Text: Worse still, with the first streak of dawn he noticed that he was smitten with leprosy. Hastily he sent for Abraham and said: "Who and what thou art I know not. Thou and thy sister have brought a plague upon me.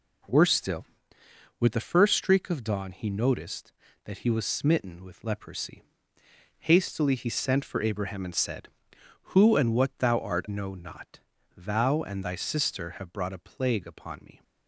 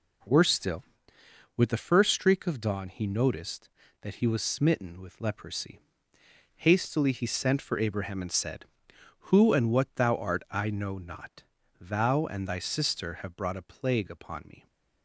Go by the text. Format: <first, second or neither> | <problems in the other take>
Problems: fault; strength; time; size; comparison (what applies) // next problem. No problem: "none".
second | skips "I"; at 10.4 s